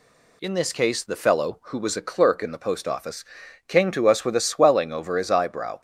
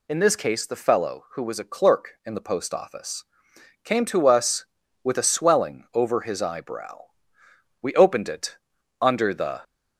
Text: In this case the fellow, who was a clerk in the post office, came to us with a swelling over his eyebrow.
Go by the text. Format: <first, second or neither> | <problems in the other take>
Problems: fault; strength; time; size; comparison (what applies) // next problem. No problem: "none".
first | goes on to say "We opened it under the"; strong; from 7.8 s on; 1.8 s long